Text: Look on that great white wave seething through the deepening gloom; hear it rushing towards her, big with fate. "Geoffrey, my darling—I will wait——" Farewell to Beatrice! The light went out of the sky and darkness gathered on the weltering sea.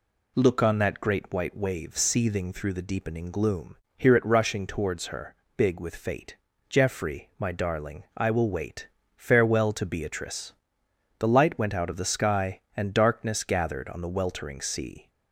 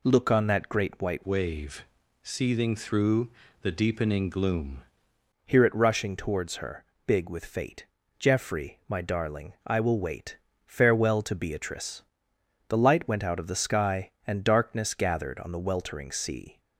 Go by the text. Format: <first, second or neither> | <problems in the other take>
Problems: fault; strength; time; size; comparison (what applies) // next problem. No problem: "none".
first | changes voice from "wave" to "gloom"; from 1.2 to 4.8 s; 3.6 s long // pauses between "wave" and "seething"; at 1.8 s; 0.40 s long // pauses between "through" and "the"; slight; at 3.2 s; 0.34 s long